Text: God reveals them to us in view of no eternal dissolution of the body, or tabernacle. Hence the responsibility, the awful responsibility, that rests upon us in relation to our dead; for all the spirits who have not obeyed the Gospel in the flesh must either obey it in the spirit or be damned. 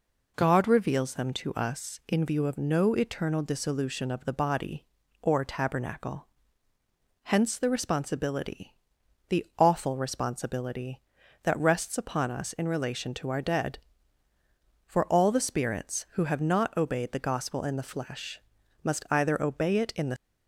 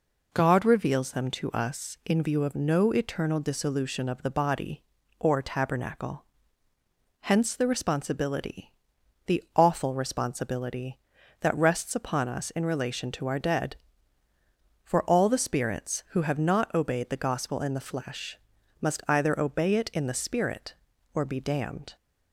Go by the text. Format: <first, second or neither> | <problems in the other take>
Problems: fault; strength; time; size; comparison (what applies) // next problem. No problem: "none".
second | pauses between "flesh" and "must"; at 18.3 s; 0.42 s long; also in the second // stops before "spirit or be damned"; at 20.1 s